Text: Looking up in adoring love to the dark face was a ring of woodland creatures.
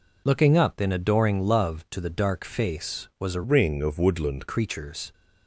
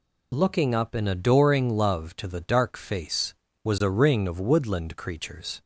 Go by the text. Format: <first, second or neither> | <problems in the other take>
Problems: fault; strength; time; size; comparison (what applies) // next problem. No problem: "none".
second | changes voice from "ring" to "woodland"; from 3.4 to 4.4 s; 1.0 s long